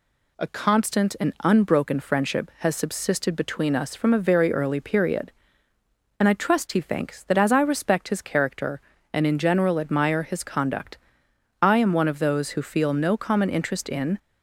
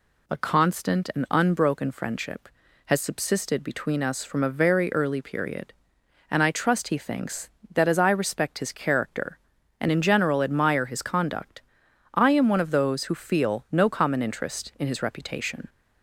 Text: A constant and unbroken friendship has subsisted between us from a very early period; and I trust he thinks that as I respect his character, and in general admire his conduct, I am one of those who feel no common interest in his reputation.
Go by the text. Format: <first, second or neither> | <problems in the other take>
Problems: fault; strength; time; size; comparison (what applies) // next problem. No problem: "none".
second | stops before "his reputation"; at 14.1 s